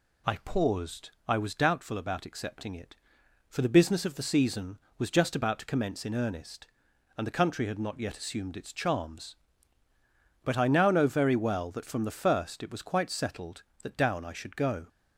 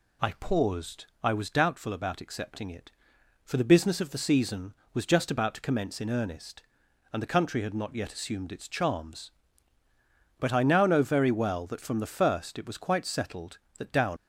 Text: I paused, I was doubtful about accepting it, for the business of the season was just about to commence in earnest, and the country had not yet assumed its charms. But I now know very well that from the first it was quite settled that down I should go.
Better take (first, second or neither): first